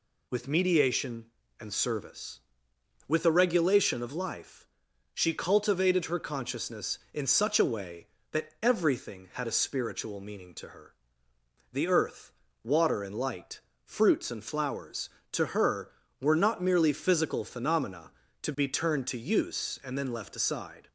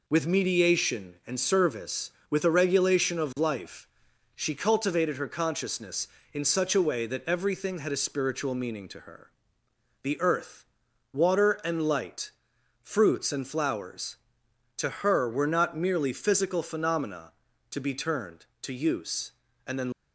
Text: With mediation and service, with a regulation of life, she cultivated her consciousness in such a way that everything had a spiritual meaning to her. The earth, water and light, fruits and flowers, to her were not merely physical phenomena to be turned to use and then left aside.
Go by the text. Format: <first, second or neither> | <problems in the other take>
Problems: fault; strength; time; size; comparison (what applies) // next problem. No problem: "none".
first | stops before "left aside"; at 19.9 s